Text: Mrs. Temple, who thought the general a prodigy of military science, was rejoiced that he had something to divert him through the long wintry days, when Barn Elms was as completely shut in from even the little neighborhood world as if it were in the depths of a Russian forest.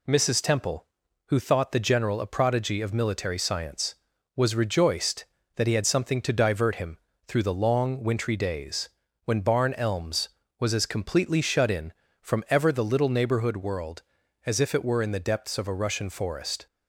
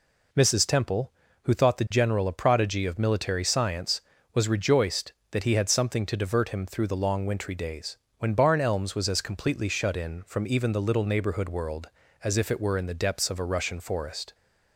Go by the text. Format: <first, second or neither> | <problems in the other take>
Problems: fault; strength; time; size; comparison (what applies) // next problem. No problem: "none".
second | pauses between "him" and "through"; slight; at 6.9 s; 0.30 s long // says "ever" for "even"; at 12.5 s